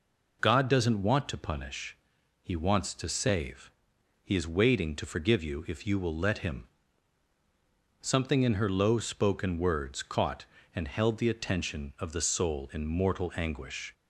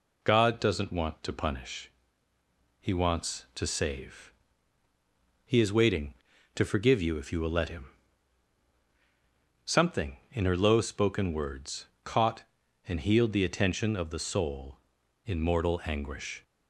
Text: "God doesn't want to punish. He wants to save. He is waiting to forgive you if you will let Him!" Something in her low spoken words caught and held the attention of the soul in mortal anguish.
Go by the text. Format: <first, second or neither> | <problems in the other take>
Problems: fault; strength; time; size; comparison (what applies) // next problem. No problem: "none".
first | pauses between "words" and "caught"; slight; at 11.8 s; 0.16 s long // says "healed" for "held"; at 13.0 s